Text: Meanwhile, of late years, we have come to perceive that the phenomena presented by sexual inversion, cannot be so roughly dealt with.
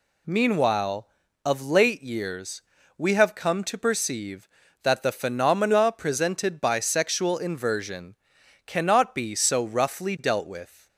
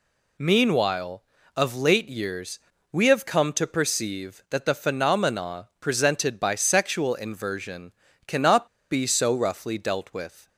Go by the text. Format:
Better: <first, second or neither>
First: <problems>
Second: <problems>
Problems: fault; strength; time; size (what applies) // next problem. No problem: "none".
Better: first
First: none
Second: pauses between "cannot" and "be"; slight; at 8.6 s; 0.25 s long